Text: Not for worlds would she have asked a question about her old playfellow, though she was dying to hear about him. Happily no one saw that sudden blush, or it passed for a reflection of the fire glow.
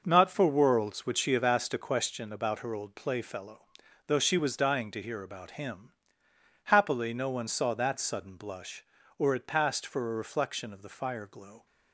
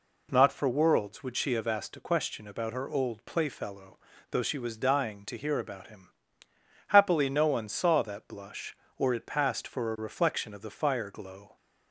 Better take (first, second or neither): first